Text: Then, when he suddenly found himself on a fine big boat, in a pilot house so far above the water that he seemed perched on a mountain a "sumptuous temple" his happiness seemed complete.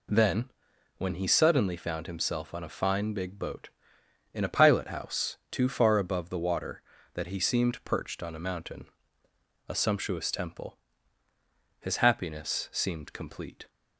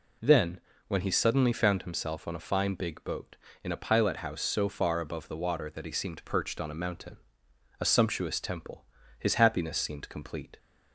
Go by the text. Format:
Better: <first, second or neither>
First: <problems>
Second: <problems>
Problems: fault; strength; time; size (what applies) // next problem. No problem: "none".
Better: second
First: says "too" for "so"; at 5.5 s // pauses between "mountain" and "a"; noticeable; at 8.8 s; 0.82 s long // pauses between "temple" and "his"; at 10.7 s; 1.0 s long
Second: pauses between "mountain" and "a"; noticeable; at 7.1 s; 0.62 s long // pauses between "temple" and "his"; slight; at 8.8 s; 0.34 s long